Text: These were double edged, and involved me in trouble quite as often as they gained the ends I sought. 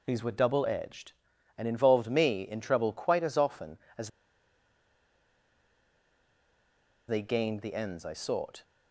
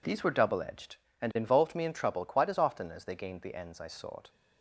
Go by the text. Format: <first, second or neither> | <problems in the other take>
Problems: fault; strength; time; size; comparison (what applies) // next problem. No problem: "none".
second | pauses between "as" and "they"; strong; at 4.1 s; 2.9 s long